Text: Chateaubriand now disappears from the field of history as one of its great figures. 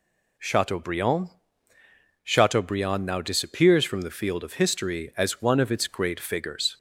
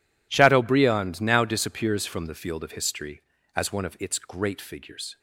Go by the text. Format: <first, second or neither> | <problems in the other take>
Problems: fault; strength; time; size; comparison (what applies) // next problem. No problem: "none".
second | says "Chateaubriand" twice; at 2.2 s